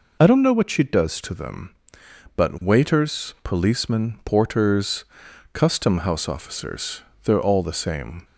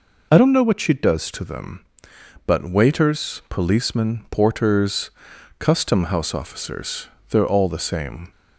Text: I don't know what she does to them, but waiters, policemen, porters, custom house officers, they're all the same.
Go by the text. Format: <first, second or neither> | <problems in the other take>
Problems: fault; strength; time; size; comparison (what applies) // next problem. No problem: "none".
neither | none